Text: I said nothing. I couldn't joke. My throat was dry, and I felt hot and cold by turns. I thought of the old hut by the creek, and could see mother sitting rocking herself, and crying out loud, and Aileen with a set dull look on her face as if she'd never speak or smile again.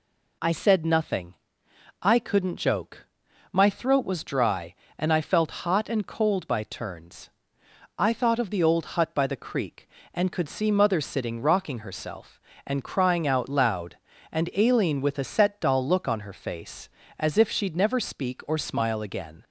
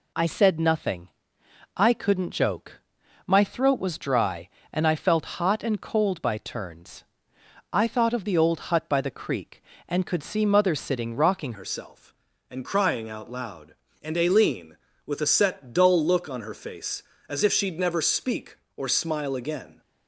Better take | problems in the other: first | changes voice at "herself"; from 11.5 s on; 8.3 s long

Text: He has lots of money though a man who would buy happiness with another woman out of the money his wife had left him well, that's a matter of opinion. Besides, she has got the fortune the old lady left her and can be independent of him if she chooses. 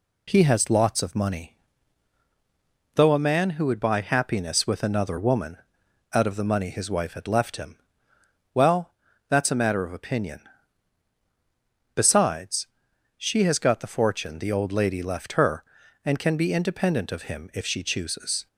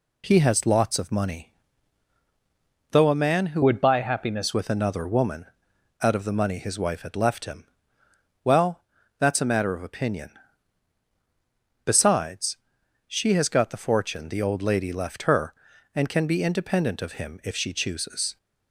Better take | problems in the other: first | pauses between "money" and "though"; strong; at 1.5 s; 1.4 s long; strong in the first // changes voice from "would" to "happiness"; from 3.6 to 4.5 s; 0.9 s long // pauses between "woman" and "out"; noticeable; at 5.4 s; 0.56 s long; noticeable in the first // pauses between "him" and "well"; noticeable; at 7.6 s; 0.80 s long; noticeable in the first

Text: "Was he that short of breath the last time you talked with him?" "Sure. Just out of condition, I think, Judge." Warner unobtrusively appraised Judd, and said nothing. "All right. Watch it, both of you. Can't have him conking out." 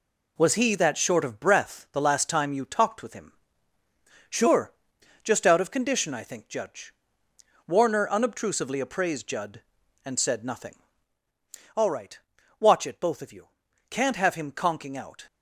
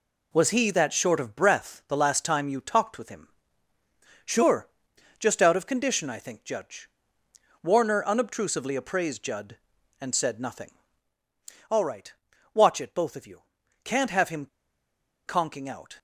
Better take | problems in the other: first | pauses between "him" and "conking"; noticeable; at 14.4 s; 0.80 s long

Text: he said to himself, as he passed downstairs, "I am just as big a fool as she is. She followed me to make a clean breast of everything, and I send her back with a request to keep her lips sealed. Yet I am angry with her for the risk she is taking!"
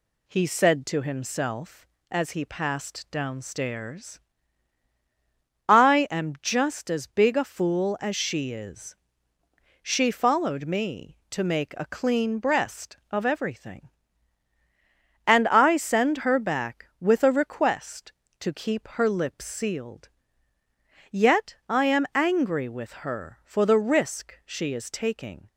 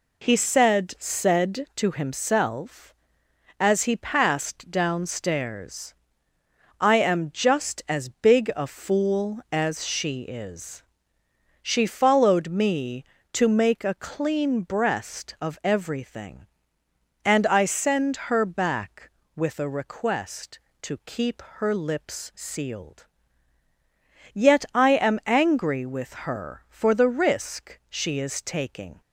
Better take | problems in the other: first | says "said" twice; at 1.0 s // pauses between "keep" and "her"; slight; at 21.4 s; 0.16 s long // pauses between "with" and "her"; slight; at 26.1 s; 0.18 s long

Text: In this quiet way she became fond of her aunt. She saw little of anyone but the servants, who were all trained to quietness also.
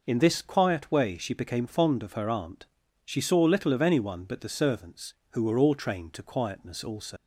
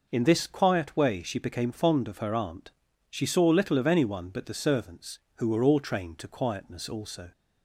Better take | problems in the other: second | leaves "also" unfinished; at 7.1 s; 100 ms

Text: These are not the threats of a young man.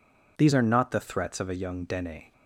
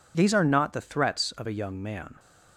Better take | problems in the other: second | says "dene" for "man"; at 1.8 s

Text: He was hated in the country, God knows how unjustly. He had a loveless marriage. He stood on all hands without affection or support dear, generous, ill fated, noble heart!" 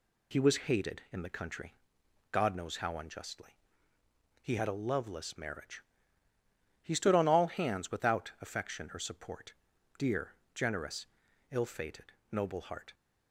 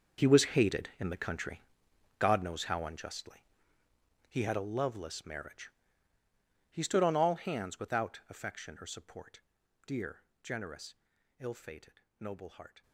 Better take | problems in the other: first | gets quieter; strong; throughout; 15.5 dB // pauses between "support" and "dear"; at 9.4 s; 0.44 s long; also in the first

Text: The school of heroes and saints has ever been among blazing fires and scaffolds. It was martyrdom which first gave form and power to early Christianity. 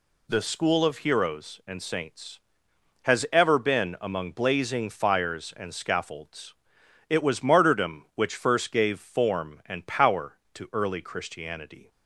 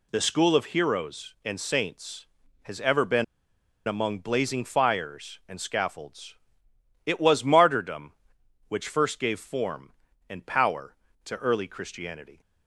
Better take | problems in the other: first | pauses between "been" and "among"; noticeable; at 3.2 s; 0.63 s long

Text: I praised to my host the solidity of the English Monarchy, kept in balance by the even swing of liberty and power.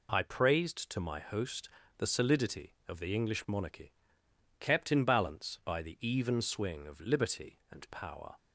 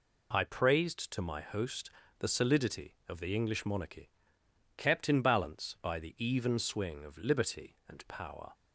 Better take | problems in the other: neither | pauses between "host" and "the"; slight; the same in both

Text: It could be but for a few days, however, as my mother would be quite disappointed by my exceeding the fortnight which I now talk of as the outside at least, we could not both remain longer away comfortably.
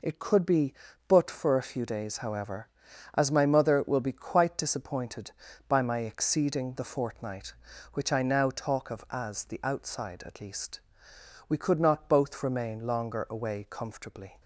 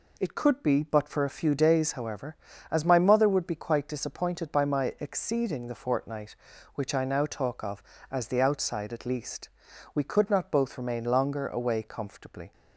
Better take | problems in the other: second | says "will" for "would"; at 3.8 s

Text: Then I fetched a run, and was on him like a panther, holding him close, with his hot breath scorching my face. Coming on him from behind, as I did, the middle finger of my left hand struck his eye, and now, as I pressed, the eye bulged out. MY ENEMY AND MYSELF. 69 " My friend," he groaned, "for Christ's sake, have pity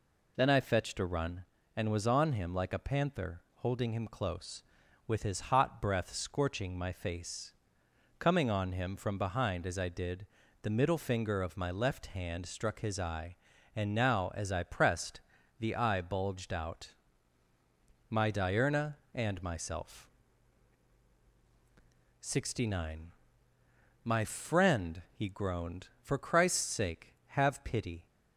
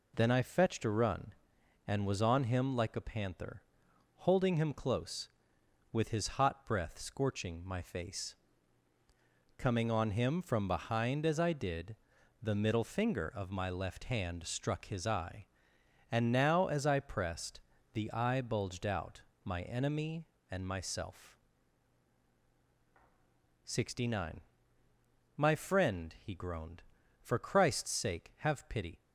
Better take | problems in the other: second | says "Diurna" for "ENEMY"; at 18.3 s

